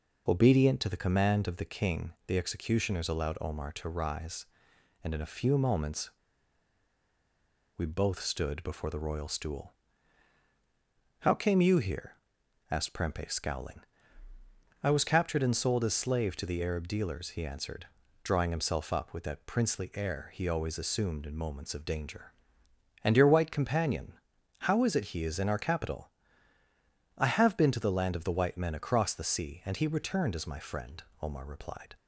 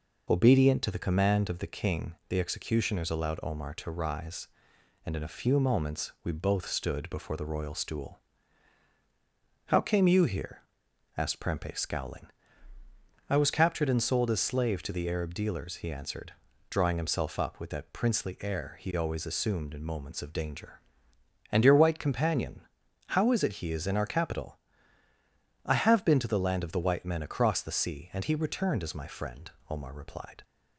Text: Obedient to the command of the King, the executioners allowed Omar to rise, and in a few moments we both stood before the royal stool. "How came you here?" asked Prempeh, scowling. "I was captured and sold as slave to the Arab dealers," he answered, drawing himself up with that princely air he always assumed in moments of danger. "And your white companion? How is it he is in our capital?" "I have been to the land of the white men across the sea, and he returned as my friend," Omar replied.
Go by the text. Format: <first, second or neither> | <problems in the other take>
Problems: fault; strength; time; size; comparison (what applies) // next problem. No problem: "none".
second | pauses between "moments" and "we"; strong; at 6.1 s; 1.6 s long